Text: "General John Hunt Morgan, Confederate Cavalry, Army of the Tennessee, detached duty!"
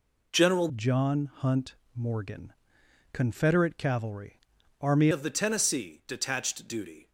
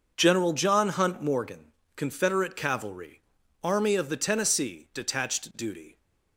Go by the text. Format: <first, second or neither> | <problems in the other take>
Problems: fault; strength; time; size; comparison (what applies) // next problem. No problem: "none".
second | changes voice from "John" to "Army"; from 0.7 to 5.0 s; 4.3 s long // pauses between "Hunt" and "Morgan"; slight; at 1.7 s; 0.20 s long